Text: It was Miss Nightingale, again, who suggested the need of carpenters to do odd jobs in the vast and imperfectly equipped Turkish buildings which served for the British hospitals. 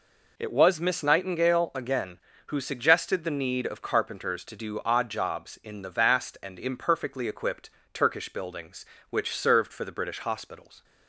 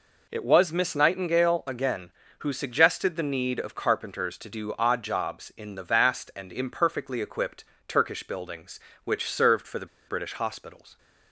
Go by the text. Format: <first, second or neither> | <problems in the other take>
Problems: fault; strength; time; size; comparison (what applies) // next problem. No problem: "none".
first | pauses between "equipped" and "Turkish"; slight; at 7.6 s; 0.24 s long; slight in the first // pauses between "the" and "British"; slight; at 9.8 s; 0.22 s long